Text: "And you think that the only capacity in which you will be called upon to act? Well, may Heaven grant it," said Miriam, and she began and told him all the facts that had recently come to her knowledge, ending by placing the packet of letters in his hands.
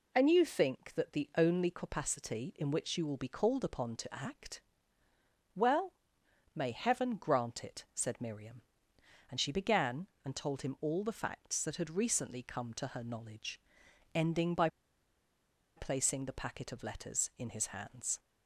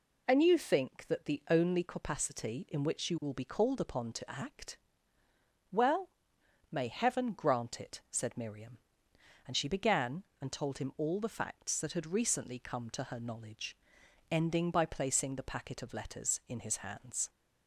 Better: second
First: pauses between "by" and "placing"; at 14.6 s; 1.0 s long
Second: none

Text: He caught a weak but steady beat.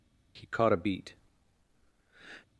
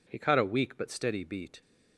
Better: second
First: skips "weak but steady"; at 0.7 s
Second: none

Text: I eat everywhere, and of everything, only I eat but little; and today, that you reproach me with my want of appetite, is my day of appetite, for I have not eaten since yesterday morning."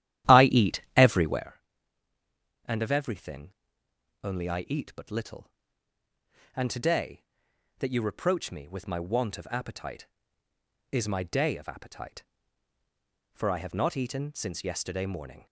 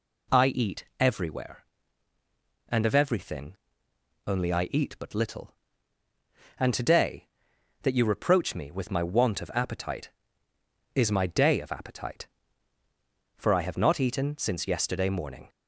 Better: second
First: starts louder than the rest; strong; until 1.5 s; 12 dB // pauses between "eat" and "everywhere"; slight; at 0.7 s; 0.16 s long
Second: pauses between "eat" and "everywhere"; slight; at 0.8 s; 0.16 s long

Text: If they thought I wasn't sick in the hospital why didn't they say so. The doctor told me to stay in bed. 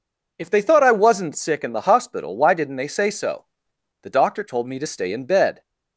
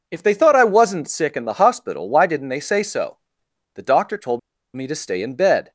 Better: first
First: none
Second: pauses between "told" and "me"; slight; at 4.3 s; 0.35 s long

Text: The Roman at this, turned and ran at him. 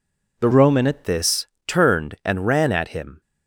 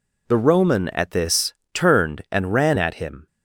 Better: second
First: changes voice from "Roman" to "at"; from 0.5 to 1.0 s; 0.5 s long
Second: none

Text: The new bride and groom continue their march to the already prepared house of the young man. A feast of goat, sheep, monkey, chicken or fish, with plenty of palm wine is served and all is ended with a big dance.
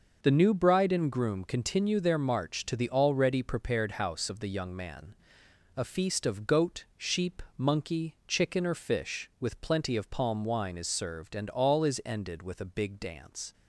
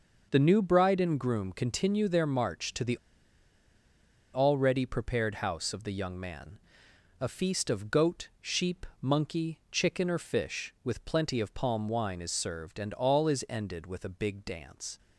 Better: first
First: none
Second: pauses between "the" and "already"; strong; at 2.9 s; 1.3 s long

